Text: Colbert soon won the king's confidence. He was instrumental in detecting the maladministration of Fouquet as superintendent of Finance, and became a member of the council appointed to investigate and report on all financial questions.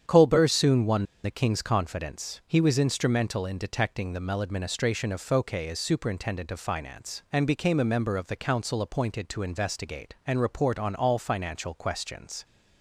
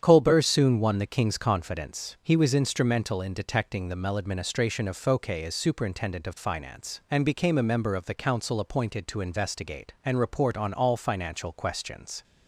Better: second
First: starts louder than the rest; strong; until 1.2 s; 8.5 dB // pauses between "won" and "the"; slight; at 1.0 s; 0.19 s long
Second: starts louder than the rest; strong; until 1.0 s; 8.5 dB

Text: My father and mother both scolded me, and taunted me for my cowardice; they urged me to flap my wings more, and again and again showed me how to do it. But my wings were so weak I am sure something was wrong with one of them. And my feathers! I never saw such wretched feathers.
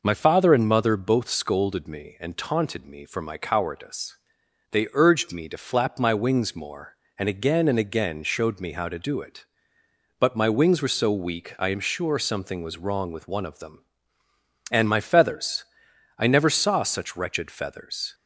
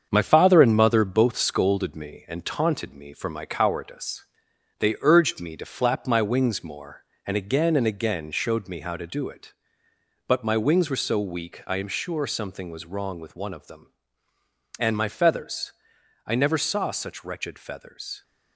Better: first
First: none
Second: gets quieter; noticeable; throughout; 5.5 dB

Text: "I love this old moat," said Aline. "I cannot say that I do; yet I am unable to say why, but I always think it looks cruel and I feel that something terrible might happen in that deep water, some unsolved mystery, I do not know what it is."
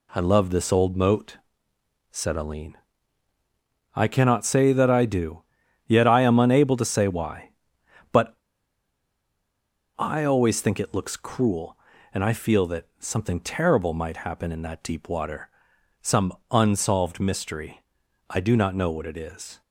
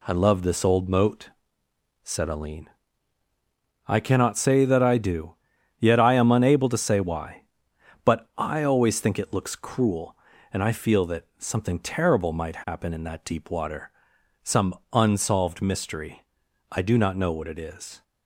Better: second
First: pauses between "but" and "I"; strong; at 8.3 s; 1.6 s long // pauses between "some" and "unsolved"; slight; at 16.3 s; 0.18 s long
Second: pauses between "some" and "unsolved"; slight; at 14.7 s; 0.18 s long

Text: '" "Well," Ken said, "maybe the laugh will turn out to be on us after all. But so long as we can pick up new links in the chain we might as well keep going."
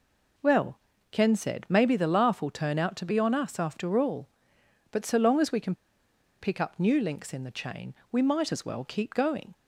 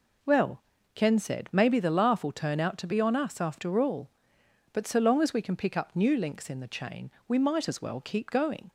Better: second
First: pauses between "can" and "pick"; noticeable; at 5.7 s; 0.66 s long // pauses between "chain" and "we"; slight; at 7.9 s; 0.18 s long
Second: pauses between "chain" and "we"; slight; at 7.1 s; 0.18 s long

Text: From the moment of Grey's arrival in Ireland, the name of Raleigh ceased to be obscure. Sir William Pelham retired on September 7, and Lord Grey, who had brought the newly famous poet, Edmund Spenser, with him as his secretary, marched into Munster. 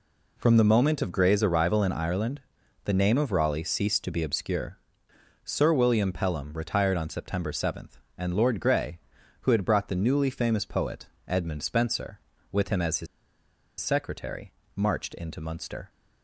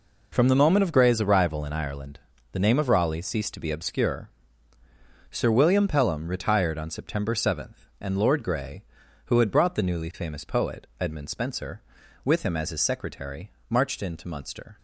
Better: second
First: pauses between "his" and "secretary"; noticeable; at 13.0 s; 0.74 s long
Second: none

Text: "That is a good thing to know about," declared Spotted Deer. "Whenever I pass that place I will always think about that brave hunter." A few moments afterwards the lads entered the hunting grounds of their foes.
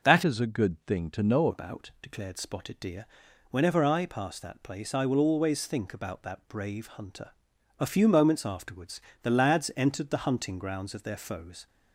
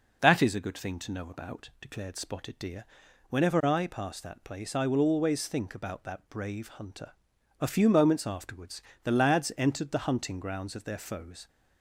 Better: second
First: changes voice from "is" to "know"; from 0.2 to 1.4 s; 1.2 s long // pauses between "afterwards" and "the"; slight; at 9.0 s; 0.18 s long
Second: pauses between "afterwards" and "the"; slight; at 8.8 s; 0.18 s long

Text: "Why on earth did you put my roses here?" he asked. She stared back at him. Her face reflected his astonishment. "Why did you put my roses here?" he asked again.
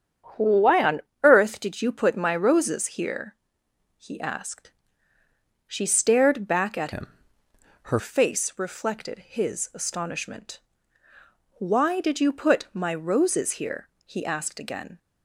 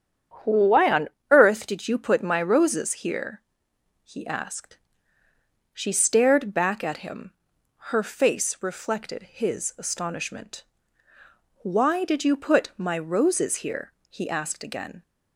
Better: second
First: starts louder than the rest; strong; until 1.5 s; 8 dB // pauses between "on" and "earth"; slight; at 1.0 s; 0.20 s long // changes voice from "him" to "Her"; from 6.9 to 7.9 s; 1.0 s long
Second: starts louder than the rest; strong; until 1.6 s; 8.5 dB // pauses between "on" and "earth"; slight; at 1.1 s; 0.20 s long

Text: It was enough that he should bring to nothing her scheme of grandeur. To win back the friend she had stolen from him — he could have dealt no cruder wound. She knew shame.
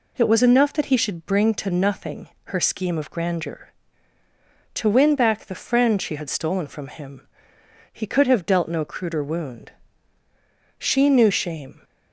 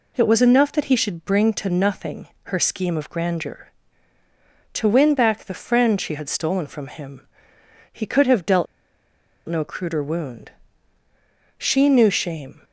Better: first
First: pauses between "nothing" and "her"; slight; at 2.2 s; 0.16 s long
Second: pauses between "nothing" and "her"; slight; at 2.2 s; 0.16 s long // pauses between "dealt" and "no"; noticeable; at 8.6 s; 0.82 s long

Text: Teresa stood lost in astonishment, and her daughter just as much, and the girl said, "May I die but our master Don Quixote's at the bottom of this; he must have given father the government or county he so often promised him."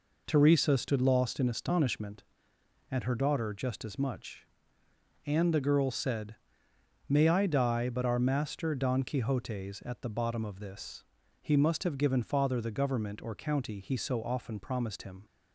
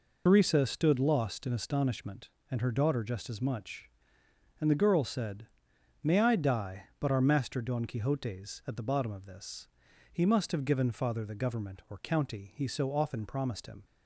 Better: first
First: none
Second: loses the start of "Teresa"; at 0.2 s; 90 ms

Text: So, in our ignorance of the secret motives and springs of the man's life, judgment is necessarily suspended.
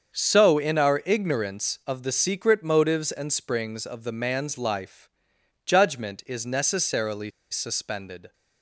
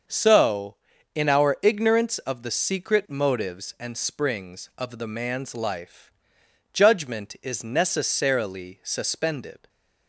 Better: second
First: starts louder than the rest; until 1.1 s; 7 dB // pauses between "necessarily" and "suspended"; slight; at 7.3 s; 0.20 s long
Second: starts louder than the rest; until 1.4 s; 6.5 dB

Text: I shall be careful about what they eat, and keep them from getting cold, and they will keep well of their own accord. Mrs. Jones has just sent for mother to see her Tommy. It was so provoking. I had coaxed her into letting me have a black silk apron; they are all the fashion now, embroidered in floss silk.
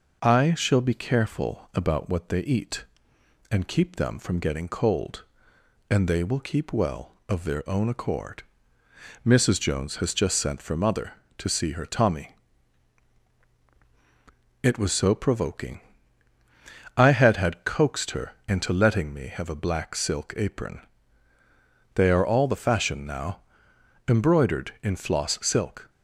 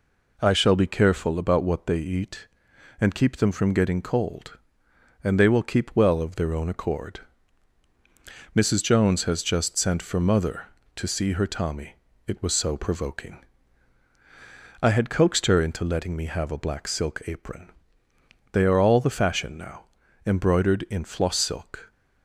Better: second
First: says "had" twice; at 17.3 s // pauses between "her" and "into"; slight; at 18.3 s; 0.16 s long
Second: none

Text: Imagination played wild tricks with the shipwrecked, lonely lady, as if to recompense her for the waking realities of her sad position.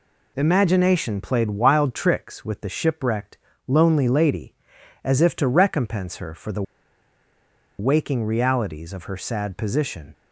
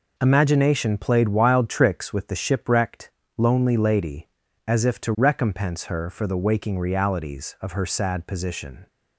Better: second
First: pauses between "the" and "waking"; at 6.6 s; 1.1 s long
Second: none

